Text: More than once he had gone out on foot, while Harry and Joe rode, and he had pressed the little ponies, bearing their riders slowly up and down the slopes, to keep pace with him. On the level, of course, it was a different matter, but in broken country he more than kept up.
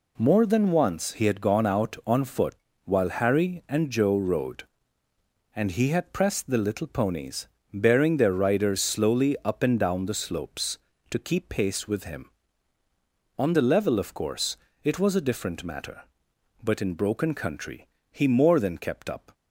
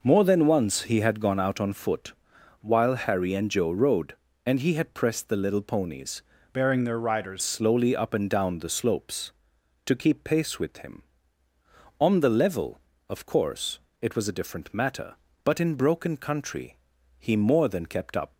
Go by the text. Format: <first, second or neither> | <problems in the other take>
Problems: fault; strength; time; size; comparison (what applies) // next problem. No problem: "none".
first | changes voice from "bearing" to "riders"; from 6.5 to 7.4 s; 0.9 s long // pauses between "country" and "he"; at 16.7 s; 0.42 s long; slight in the first